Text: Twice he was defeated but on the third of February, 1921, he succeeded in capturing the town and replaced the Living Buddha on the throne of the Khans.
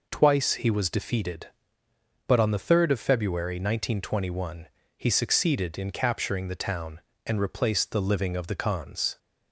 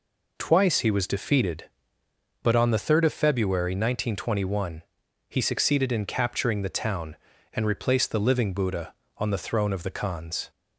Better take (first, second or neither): second